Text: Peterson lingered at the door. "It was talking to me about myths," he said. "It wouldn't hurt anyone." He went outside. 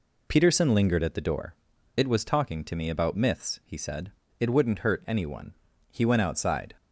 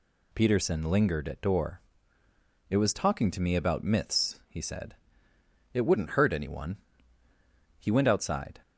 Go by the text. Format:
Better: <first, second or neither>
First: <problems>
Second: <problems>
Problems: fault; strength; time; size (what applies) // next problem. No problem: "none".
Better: first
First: none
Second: skips "the"; at 1.4 s